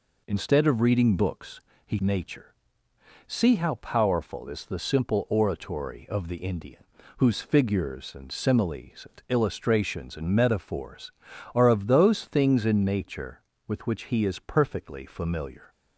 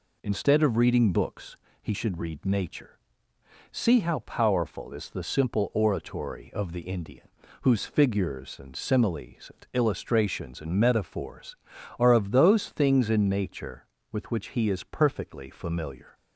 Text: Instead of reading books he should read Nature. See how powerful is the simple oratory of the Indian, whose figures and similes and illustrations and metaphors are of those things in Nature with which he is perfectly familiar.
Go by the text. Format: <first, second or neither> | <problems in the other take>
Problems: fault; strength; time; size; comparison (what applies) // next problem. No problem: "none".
second | pauses between "books" and "he"; slight; at 1.5 s; 0.26 s long; slight in the second // skips "should read"; at 1.9 s